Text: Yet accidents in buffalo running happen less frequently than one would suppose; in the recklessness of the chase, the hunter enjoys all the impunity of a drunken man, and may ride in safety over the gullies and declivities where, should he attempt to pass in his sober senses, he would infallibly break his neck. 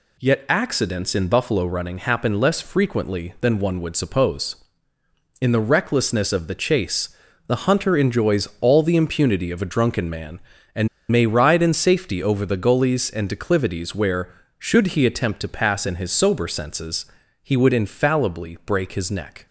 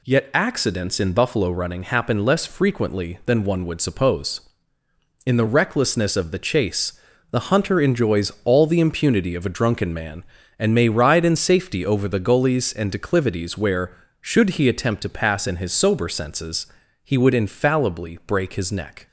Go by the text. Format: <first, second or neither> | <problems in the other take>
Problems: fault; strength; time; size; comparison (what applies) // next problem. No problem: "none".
second | pauses between "and" and "may"; slight; at 10.8 s; 0.23 s long